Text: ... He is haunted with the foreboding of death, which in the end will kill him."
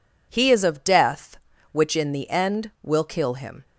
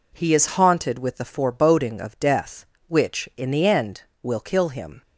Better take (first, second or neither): second